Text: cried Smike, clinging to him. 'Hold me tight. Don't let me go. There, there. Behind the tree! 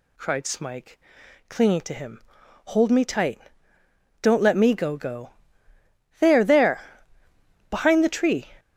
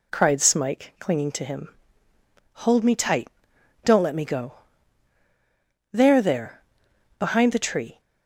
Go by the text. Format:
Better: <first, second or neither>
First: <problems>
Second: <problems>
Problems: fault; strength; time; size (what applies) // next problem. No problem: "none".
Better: second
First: says "go" twice; at 4.9 s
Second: none